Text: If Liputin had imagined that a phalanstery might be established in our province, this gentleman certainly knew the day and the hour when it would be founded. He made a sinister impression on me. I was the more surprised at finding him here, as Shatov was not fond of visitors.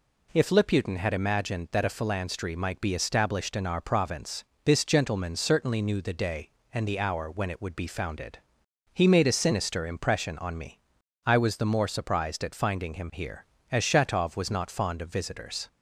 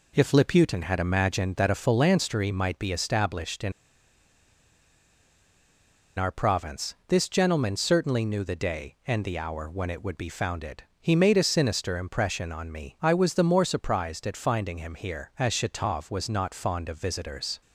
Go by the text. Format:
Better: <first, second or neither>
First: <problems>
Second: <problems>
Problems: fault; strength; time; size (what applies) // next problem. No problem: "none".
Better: first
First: none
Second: pauses between "in" and "our"; strong; at 3.7 s; 2.4 s long